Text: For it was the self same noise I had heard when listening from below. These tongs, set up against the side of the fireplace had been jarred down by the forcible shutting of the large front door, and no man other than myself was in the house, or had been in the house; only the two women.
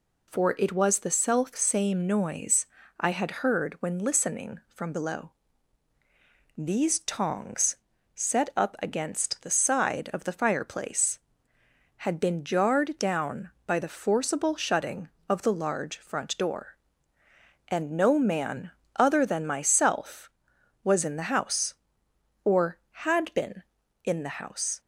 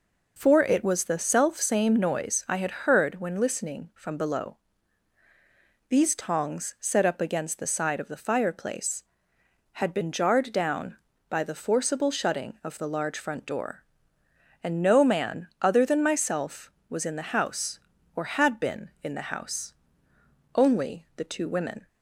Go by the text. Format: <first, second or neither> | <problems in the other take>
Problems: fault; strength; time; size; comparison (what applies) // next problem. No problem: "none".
second | pauses between "noise" and "I"; slight; at 2.6 s; 0.34 s long // pauses between "man" and "other"; slight; at 18.7 s; 0.26 s long // stops before "only the two women"; at 24.7 s